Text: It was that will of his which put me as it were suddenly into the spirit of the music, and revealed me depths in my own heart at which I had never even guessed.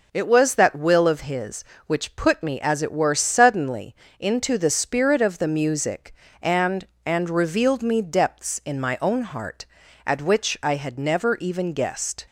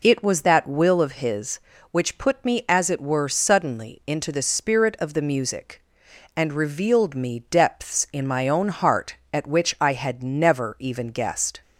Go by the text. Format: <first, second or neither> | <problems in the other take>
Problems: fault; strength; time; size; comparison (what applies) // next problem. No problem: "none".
second | pauses between "suddenly" and "into"; slight; at 3.9 s; 0.24 s long // says "and" twice; at 7.0 s